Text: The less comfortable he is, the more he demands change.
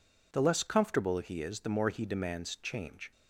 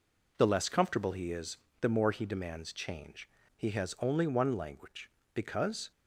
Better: first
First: none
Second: goes on to say "He has only one language because"; strong; from 3.5 s on; 2.3 s long

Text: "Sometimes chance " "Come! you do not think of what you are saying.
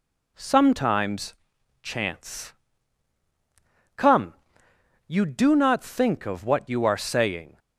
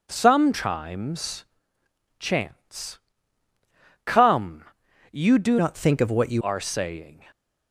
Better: first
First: pauses between "Sometimes" and "chance"; noticeable; at 1.3 s; 0.48 s long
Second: pauses between "Sometimes" and "chance"; noticeable; at 1.4 s; 0.72 s long // changes voice from "not" to "you"; from 5.5 to 6.4 s; 0.9 s long

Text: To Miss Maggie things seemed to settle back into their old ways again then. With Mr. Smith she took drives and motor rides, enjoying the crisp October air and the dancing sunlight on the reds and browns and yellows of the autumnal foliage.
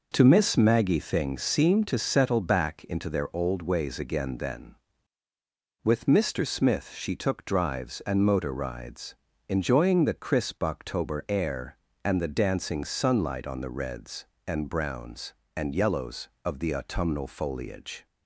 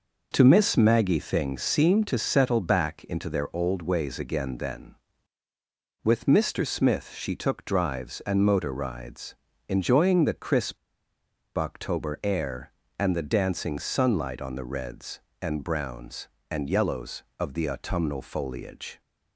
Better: first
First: none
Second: pauses between "crisp" and "October"; noticeable; at 10.7 s; 0.80 s long

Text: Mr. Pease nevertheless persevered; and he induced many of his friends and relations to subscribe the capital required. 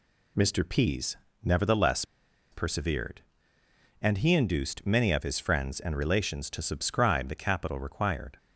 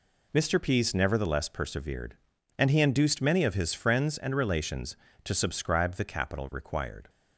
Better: second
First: pauses between "Pease" and "nevertheless"; slight; at 1.1 s; 0.30 s long // pauses between "nevertheless" and "persevered"; noticeable; at 2.0 s; 0.48 s long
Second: none

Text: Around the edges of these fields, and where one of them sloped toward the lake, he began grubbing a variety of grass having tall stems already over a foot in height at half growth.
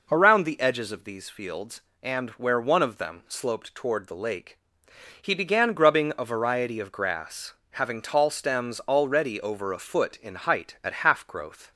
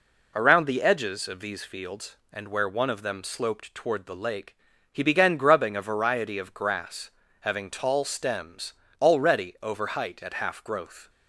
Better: first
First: pauses between "grass" and "having"; slight; at 7.5 s; 0.18 s long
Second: pauses between "grass" and "having"; slight; at 7.1 s; 0.30 s long // pauses between "stems" and "already"; slight; at 8.7 s; 0.30 s long // skips "a foot in"; at 9.8 s

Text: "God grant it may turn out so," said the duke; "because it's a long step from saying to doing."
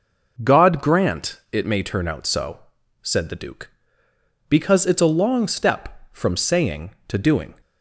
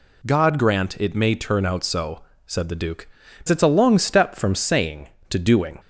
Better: first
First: none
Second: skips "because"; at 3.2 s

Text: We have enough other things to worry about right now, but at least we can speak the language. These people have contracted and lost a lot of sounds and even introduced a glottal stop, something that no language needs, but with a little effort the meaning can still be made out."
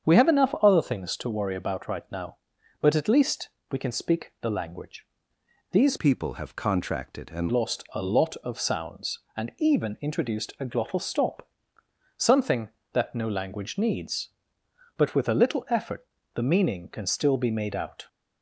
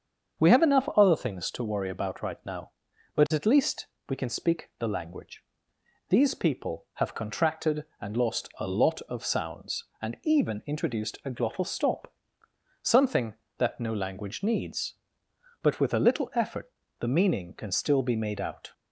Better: second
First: starts louder than the rest; strong; until 1.1 s; 7.5 dB // pauses between "least" and "we"; slight; at 3.4 s; 0.22 s long // changes voice from "people" to "and"; from 5.9 to 7.4 s; 1.5 s long // pauses between "effort" and "the"; slight; at 16.0 s; 0.30 s long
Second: starts louder than the rest; until 1.5 s; 7 dB // pauses between "least" and "we"; slight; at 3.8 s; 0.22 s long // pauses between "effort" and "the"; slight; at 16.7 s; 0.30 s long

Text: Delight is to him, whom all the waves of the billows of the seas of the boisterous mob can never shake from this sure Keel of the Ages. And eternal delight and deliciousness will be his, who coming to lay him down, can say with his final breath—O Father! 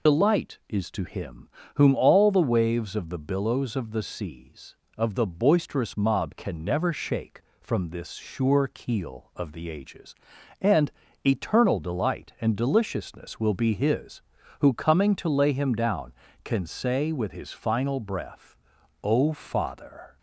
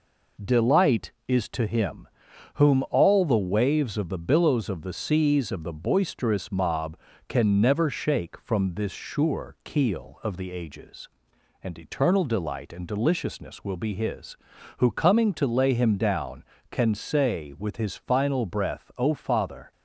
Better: second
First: loses the start of "Delight"; at 0.0 s; 55 ms // pauses between "And" and "eternal"; slight; at 10.9 s; 0.34 s long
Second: none

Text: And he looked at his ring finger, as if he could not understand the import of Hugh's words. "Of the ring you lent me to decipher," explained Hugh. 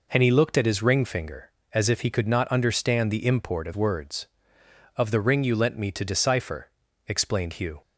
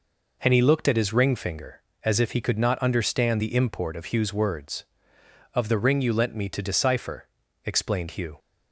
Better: second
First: skips "Hugh's"; at 3.7 s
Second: none

